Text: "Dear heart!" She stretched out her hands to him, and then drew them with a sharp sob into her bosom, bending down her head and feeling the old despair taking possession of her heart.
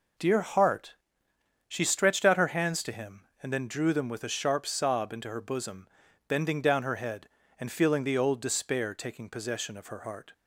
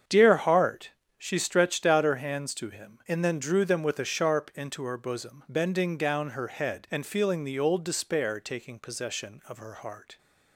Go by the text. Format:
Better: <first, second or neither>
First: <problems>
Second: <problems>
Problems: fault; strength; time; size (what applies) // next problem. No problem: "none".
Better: first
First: none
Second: starts louder than the rest; strong; until 1.3 s; 7.5 dB // skips "sob"; at 4.5 s